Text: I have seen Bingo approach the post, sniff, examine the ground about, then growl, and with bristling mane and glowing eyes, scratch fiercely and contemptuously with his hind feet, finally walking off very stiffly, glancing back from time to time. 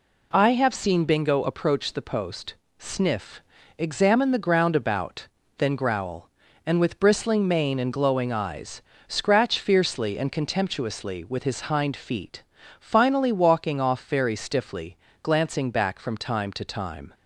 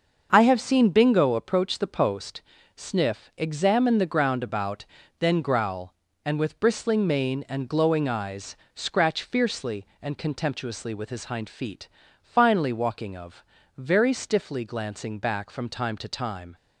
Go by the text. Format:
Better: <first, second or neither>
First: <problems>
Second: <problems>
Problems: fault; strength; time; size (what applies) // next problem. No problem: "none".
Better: first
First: none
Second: starts louder than the rest; until 1.3 s; 6.5 dB // says "of" for "off"; at 13.1 s